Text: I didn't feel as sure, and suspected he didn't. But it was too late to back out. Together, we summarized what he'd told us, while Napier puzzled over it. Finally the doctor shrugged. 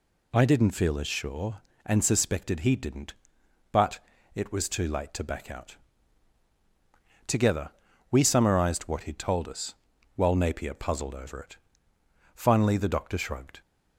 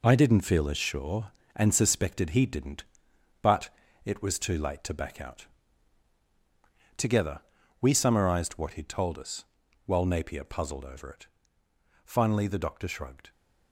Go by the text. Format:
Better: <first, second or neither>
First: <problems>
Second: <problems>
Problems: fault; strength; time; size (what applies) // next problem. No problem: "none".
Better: first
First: pauses between "But" and "it"; slight; at 3.9 s; 0.36 s long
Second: gets quieter; strong; throughout; 7.5 dB // pauses between "But" and "it"; slight; at 3.6 s; 0.36 s long